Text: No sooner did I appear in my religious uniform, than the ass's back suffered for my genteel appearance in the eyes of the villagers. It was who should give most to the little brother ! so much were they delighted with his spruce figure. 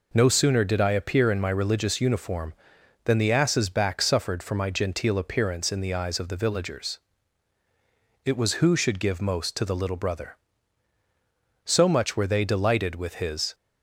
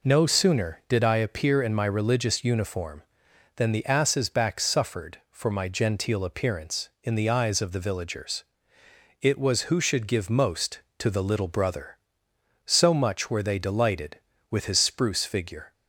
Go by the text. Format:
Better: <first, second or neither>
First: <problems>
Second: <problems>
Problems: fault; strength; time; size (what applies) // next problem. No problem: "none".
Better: second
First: stops before "spruce figure"; at 13.5 s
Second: none